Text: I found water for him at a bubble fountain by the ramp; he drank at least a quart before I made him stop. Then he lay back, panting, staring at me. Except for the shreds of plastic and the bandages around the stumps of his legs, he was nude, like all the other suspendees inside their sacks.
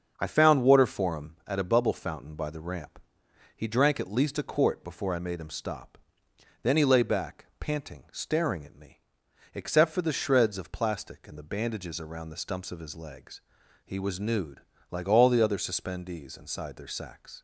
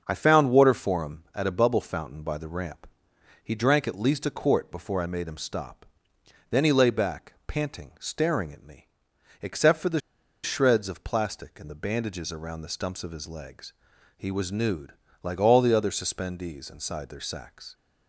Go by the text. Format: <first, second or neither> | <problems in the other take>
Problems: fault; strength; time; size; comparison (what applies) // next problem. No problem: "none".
first | starts louder than the rest; until 1.0 s; 6.5 dB; also in the first // pauses between "the" and "shreds"; at 10.0 s; 0.43 s long